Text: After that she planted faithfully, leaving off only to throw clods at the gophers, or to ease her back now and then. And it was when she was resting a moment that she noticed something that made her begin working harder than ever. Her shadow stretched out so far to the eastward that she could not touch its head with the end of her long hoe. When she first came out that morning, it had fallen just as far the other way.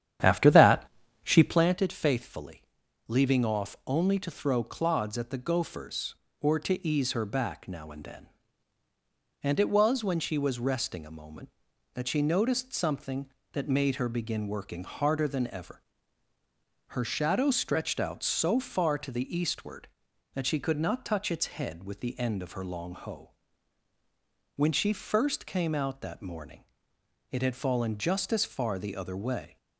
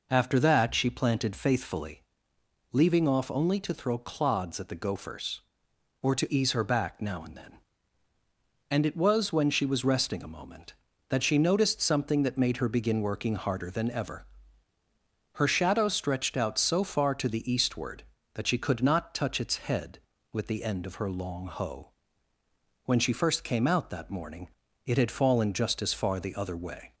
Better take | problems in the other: second | starts louder than the rest; strong; until 1.7 s; 10 dB // pauses between "that" and "she"; at 0.8 s; 0.38 s long

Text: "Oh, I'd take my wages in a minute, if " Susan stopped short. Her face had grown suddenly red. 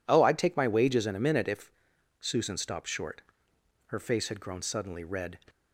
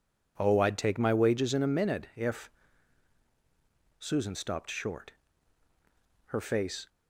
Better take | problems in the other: first | stops before "had grown suddenly red"; at 6.8 s

